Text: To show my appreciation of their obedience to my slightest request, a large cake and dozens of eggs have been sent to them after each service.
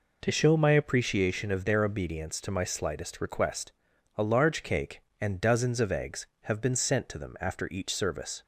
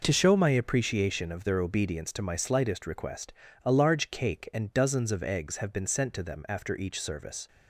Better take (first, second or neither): neither